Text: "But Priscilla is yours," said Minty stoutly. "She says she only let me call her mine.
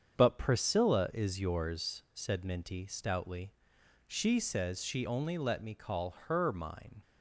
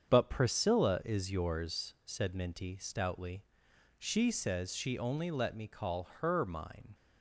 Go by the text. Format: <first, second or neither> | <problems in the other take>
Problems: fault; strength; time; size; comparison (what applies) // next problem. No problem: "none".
neither | starts louder than the rest; strong; the same in both // pauses between "call" and "her"; slight; the same in both